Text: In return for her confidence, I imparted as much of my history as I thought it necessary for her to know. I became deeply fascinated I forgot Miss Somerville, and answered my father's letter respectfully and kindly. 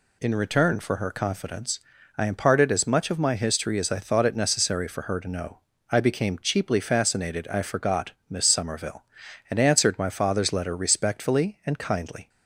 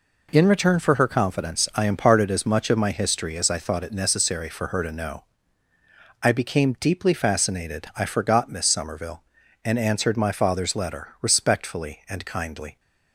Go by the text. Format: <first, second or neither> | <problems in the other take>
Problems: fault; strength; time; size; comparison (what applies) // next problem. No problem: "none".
second | says "cheaply" for "deeply"; at 6.3 s // pauses between "forgot" and "Miss"; slight; at 8.1 s; 0.18 s long